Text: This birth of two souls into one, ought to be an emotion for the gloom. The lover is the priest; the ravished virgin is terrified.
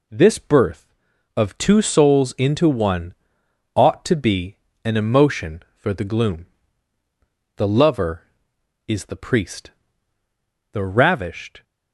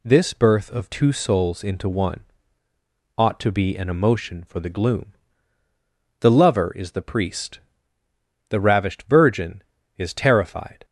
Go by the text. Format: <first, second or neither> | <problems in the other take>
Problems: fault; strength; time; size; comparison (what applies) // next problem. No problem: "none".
second | pauses between "be" and "an"; slight; at 4.5 s; 0.28 s long // stops before "virgin is terrified"; at 11.6 s